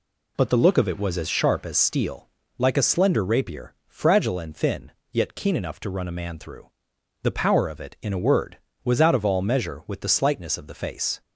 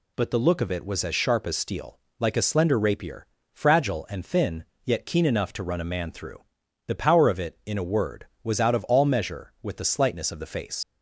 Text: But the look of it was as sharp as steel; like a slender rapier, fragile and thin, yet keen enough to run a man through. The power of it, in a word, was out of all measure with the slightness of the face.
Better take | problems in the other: first | leaves "face" unfinished; at 10.8 s; 90 ms

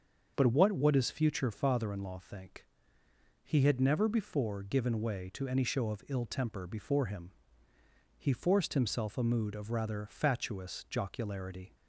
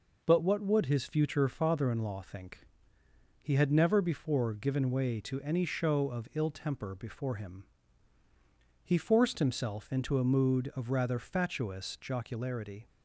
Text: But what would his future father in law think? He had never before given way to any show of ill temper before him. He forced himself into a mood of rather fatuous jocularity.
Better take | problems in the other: second | starts louder than the rest; until 1.3 s; 6.5 dB // skips "into"; at 9.1 s

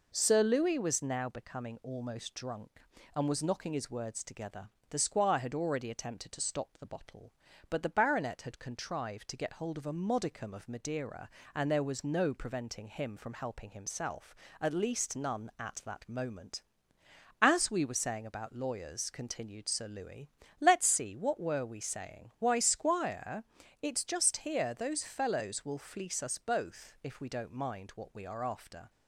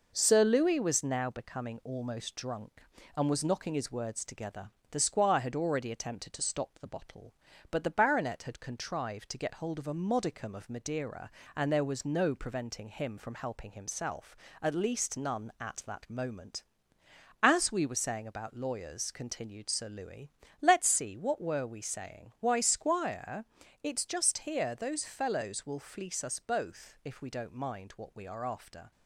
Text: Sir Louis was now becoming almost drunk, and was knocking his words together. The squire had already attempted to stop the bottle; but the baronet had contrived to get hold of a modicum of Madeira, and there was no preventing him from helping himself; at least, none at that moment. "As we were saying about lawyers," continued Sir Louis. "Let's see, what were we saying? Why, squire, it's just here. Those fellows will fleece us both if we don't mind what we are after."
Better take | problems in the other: first | gets quieter; slight; throughout; 2.5 dB

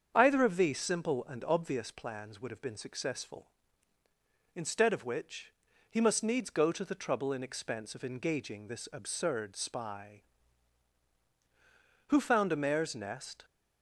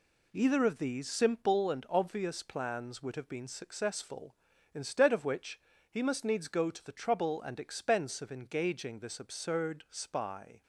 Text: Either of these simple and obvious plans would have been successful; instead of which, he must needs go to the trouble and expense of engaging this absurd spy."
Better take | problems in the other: second | starts louder than the rest; strong; until 1.1 s; 7.5 dB // goes on to say "Who found a mare's nest"; from 12.0 s on; 1.3 s long

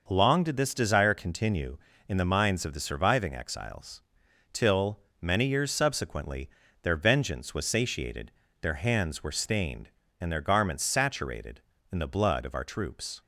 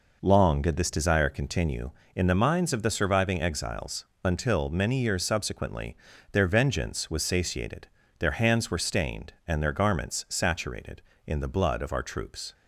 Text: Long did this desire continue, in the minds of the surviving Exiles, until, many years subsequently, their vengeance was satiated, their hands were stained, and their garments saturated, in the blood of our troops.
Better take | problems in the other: second | says "till" for "until"; at 4.5 s

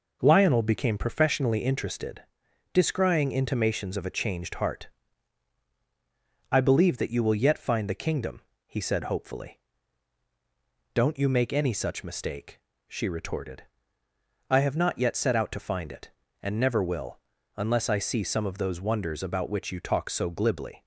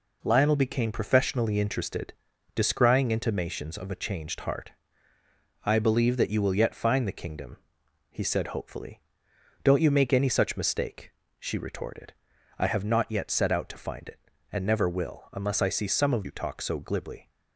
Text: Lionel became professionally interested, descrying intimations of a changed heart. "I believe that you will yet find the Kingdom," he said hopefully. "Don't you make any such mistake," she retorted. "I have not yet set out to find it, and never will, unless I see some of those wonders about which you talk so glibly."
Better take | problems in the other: first | skips "those wonders about which"; at 16.2 s

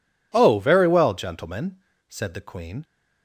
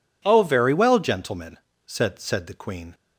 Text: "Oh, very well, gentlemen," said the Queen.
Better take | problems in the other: first | says "said" twice; at 2.2 s

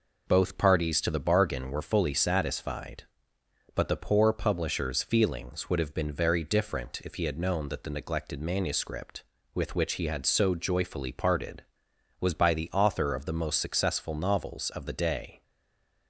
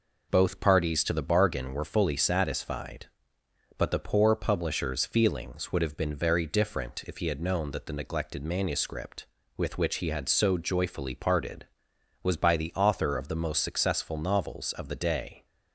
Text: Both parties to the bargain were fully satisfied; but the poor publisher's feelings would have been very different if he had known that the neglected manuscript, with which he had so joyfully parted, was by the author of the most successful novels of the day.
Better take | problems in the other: second | stays silent after the last word; slight; from 15.4 s on; 0.6 s long

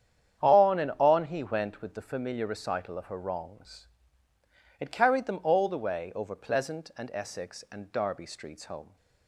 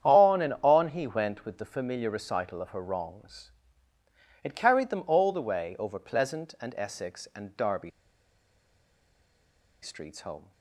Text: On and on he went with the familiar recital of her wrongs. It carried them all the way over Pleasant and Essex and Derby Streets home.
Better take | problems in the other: first | starts louder than the rest; strong; until 1.1 s; 9 dB; strong in the first // pauses between "Derby" and "Streets"; strong; at 7.9 s; 1.9 s long

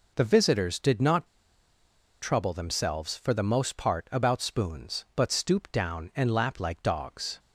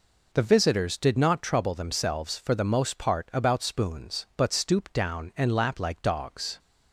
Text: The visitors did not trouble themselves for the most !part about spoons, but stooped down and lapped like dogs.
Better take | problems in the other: second | pauses between "not" and "trouble"; noticeable; at 1.2 s; 0.96 s long

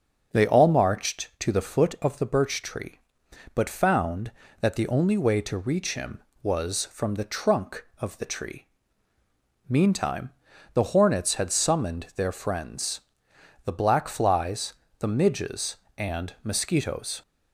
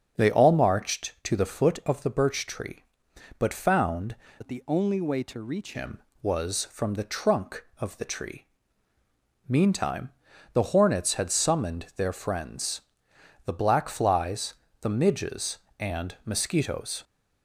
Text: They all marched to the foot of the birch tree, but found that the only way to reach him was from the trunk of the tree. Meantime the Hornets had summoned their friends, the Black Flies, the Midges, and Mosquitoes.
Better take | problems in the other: first | starts louder than the rest; until 1.2 s; 7 dB; also in the first // changes voice from "that" to "reach"; from 4.4 to 5.7 s; 1.3 s long // pauses between "Meantime" and "the"; at 10.0 s; 0.44 s long; also in the first

